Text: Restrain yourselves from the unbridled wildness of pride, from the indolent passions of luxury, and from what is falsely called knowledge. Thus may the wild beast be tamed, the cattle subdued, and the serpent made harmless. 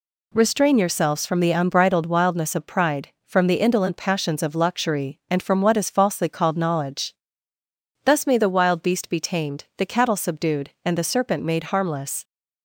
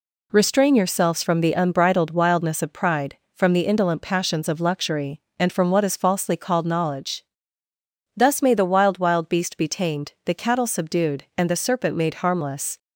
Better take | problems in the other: first | says "wild" twice; at 8.9 s

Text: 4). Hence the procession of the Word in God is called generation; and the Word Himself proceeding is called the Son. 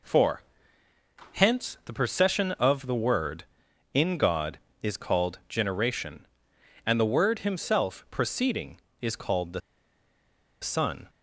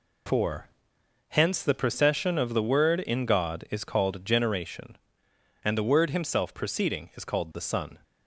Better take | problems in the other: second | pauses between "the" and "Son"; at 9.6 s; 1.0 s long

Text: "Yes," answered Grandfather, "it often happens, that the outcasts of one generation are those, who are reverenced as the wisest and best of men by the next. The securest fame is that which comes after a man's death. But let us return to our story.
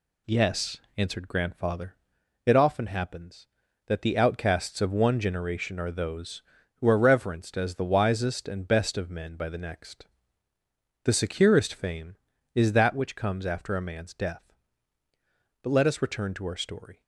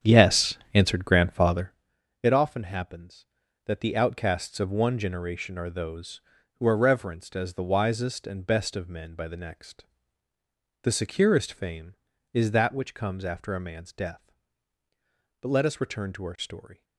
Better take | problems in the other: first | starts louder than the rest; strong; until 1.9 s; 9 dB

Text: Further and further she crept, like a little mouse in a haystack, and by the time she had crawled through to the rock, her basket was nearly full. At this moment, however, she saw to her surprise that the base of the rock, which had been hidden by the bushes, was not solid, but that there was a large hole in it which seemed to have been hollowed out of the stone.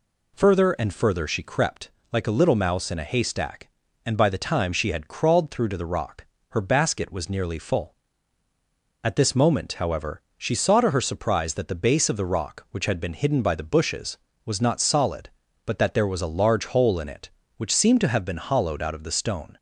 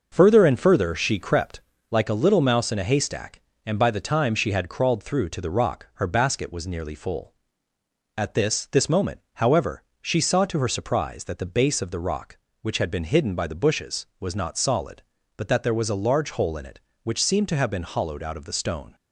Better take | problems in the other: first | says "this" twice; at 8.7 s

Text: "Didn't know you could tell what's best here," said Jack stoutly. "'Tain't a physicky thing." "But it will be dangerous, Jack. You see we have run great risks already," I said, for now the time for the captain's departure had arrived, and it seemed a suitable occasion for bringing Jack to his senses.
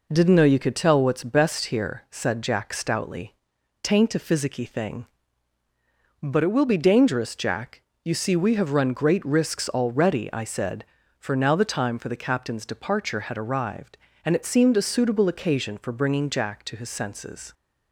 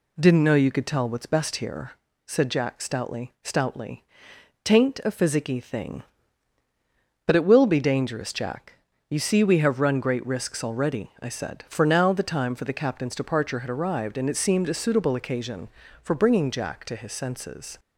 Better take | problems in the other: first | says "stoutly" twice; at 3.4 s

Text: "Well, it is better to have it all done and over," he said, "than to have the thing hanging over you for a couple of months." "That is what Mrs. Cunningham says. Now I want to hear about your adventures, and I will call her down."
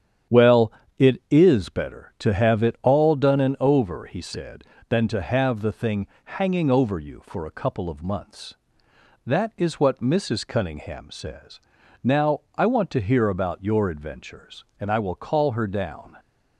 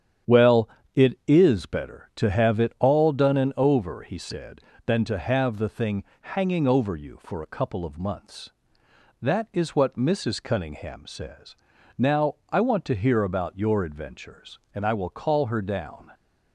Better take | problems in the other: neither | starts louder than the rest; strong; the same in both // pauses between "thing" and "hanging"; slight; the same in both

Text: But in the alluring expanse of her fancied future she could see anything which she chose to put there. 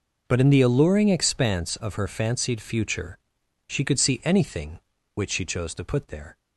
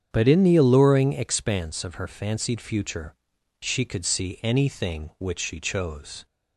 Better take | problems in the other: first | starts louder than the rest; strong; until 1.1 s; 8 dB // pauses between "future" and "she"; noticeable; at 3.1 s; 0.46 s long; noticeable in the first // stops before "to put there"; at 6.2 s

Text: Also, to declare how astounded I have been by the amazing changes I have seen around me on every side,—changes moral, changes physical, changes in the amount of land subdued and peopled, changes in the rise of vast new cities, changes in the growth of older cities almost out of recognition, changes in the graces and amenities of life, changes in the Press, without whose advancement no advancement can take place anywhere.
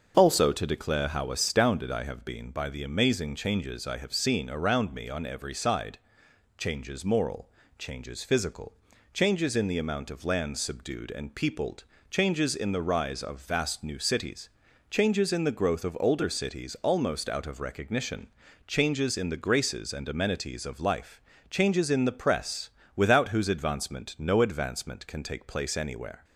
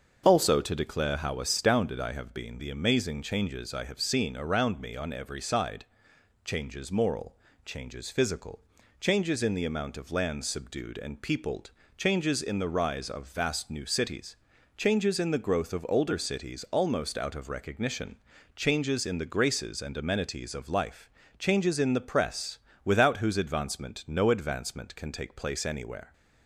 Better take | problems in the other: first | starts louder than the rest; until 1.2 s; 6.5 dB; also in the first // skips "by"; at 2.5 s

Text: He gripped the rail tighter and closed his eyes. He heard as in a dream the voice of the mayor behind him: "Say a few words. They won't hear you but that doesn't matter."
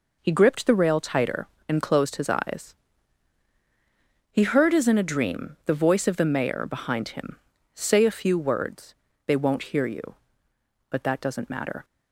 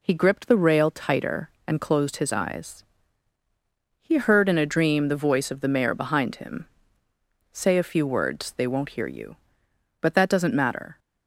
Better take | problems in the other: first | skips "as"; at 4.4 s

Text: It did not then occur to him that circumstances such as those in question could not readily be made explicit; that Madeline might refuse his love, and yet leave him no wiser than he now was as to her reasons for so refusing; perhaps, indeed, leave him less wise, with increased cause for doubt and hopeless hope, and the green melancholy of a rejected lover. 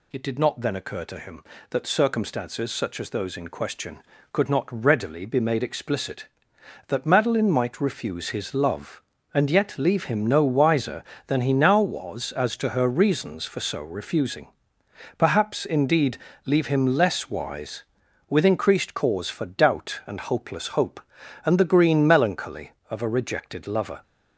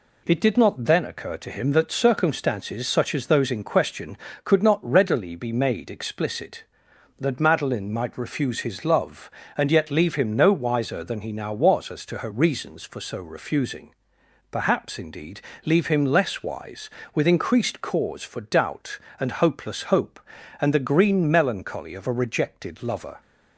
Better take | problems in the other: neither | none

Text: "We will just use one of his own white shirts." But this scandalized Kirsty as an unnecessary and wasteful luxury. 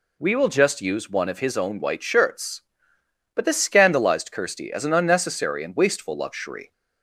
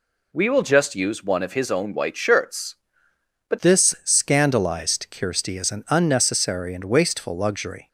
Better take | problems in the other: first | changes voice at "this"; from 3.5 s on; 4.3 s long

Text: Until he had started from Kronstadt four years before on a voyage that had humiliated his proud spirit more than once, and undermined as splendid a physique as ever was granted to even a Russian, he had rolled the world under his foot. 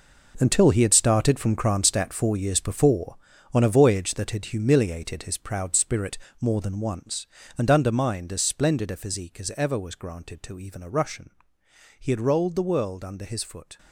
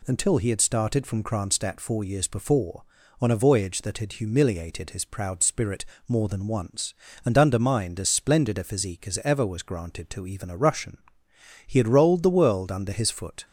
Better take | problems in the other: second | gets quieter; strong; throughout; 12 dB // pauses between "spirit" and "more"; slight; at 6.1 s; 0.24 s long; slight in the second

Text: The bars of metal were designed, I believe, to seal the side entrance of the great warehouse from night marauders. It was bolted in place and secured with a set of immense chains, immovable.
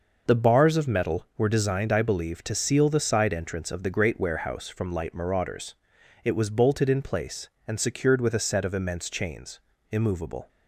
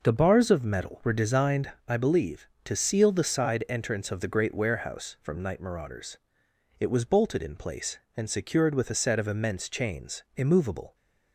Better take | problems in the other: second | says "light" for "night"; at 4.9 s

